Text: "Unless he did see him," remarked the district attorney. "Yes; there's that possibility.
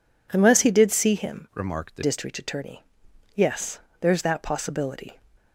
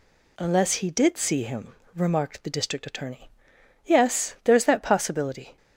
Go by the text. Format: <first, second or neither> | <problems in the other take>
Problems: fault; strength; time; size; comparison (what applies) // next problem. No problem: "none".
second | changes voice from "remarked" to "the"; from 1.5 to 2.0 s; 0.5 s long